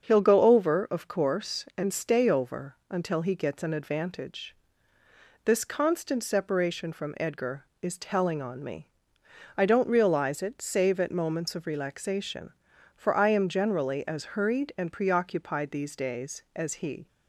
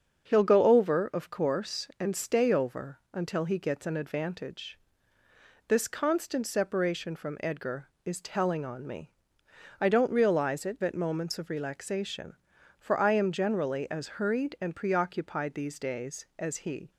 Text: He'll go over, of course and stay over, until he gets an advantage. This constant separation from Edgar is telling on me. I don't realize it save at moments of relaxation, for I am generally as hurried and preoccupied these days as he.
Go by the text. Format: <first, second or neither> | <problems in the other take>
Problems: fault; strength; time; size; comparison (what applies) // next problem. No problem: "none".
first | starts louder than the rest; until 1.3 s; 7 dB; also in the first // skips "save"; at 10.8 s